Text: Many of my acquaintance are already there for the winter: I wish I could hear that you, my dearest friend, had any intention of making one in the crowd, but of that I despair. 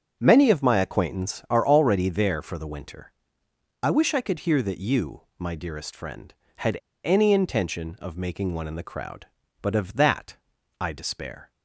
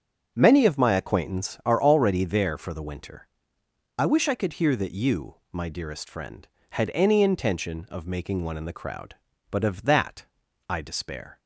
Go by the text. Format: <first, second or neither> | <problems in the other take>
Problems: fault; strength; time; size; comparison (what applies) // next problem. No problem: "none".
second | starts louder than the rest; until 1.2 s; 7 dB; also in the second // pauses between "had" and "any"; slight; at 6.7 s; 0.26 s long // pauses between "that" and "I"; at 10.3 s; 0.42 s long; also in the second